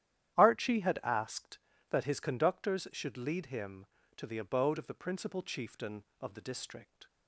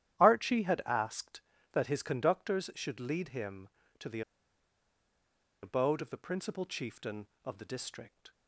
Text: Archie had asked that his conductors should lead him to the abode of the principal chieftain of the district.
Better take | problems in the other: first | starts louder than the rest; strong; until 1.2 s; 11.5 dB; strong in the first // pauses between "the" and "abode"; strong; at 4.2 s; 1.4 s long

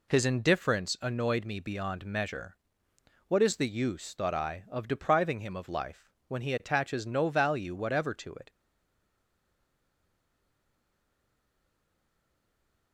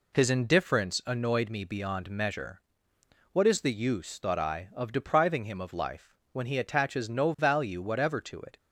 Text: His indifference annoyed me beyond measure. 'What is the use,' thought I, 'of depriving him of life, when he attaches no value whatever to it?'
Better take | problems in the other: second | stays silent after the last word; strong; from 8.5 s on; 4.4 s long

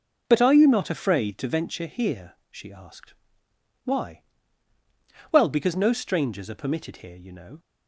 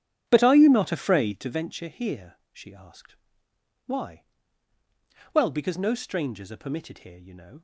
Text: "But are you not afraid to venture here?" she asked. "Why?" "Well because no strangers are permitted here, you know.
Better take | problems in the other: first | starts louder than the rest; strong; until 1.6 s; 9.5 dB

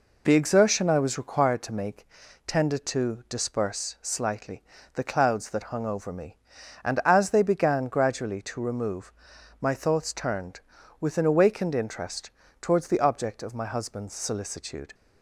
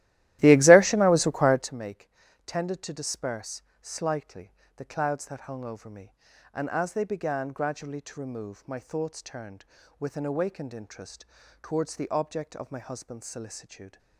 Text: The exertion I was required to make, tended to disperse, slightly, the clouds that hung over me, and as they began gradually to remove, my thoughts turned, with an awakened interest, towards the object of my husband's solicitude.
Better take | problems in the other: first | starts louder than the rest; strong; until 1.7 s; 15 dB

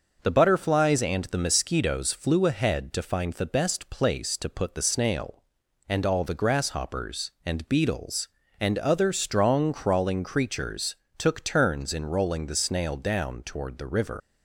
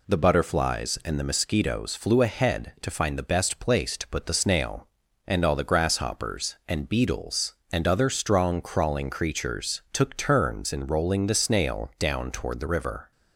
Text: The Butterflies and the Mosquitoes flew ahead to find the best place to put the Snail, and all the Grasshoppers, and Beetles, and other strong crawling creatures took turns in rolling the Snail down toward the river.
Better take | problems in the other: second | pauses between "creatures" and "took"; slight; at 10.9 s; 0.22 s long // leaves "river" unfinished; at 14.2 s; 120 ms

